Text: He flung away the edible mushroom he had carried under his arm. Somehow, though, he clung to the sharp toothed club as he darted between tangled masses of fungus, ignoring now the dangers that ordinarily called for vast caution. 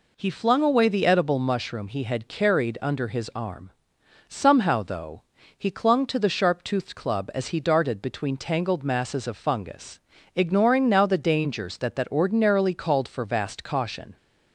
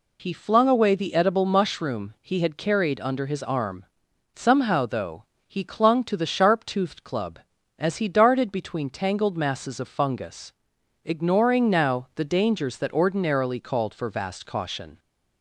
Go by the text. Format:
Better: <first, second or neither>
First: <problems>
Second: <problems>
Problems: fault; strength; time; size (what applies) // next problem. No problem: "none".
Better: second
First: says "that" twice; at 11.9 s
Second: none